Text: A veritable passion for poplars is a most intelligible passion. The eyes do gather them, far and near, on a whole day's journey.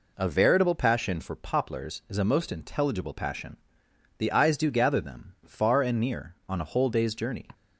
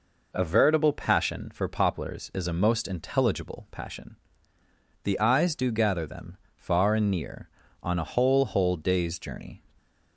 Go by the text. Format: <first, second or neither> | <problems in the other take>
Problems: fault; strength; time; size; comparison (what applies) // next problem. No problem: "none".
first | says "whole" twice; at 8.4 s